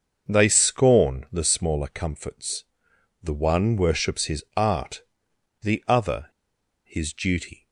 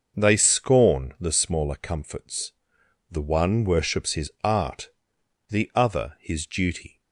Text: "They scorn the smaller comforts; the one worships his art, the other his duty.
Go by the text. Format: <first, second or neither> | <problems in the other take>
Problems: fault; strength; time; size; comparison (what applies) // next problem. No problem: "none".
second | starts louder than the rest; until 1.3 s; 6.5 dB; also in the second // pauses between "other" and "his"; noticeable; at 6.2 s; 0.57 s long